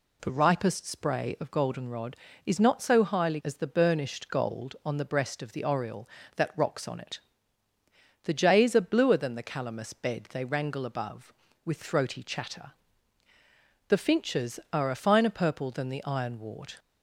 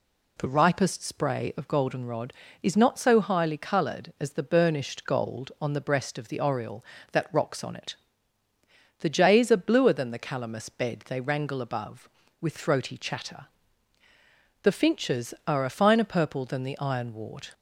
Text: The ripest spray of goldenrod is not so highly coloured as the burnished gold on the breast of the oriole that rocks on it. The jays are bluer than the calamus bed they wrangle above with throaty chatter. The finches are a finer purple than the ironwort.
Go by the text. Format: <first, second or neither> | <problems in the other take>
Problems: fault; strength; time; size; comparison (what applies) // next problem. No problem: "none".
second | skips "coloured"; at 3.4 s